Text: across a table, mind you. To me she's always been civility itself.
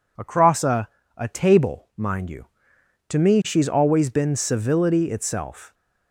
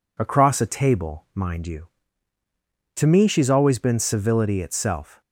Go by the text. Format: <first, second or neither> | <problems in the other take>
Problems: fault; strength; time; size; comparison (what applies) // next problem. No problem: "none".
second | says "a" twice; at 1.1 s